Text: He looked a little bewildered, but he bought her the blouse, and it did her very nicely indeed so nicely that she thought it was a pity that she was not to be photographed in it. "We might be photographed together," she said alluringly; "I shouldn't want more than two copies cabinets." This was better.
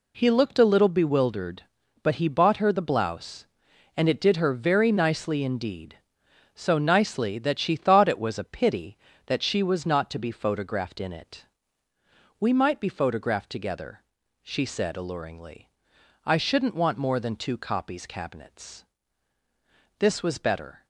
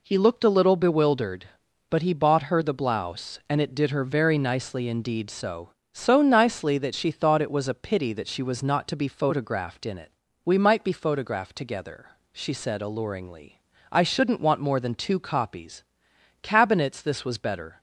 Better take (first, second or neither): first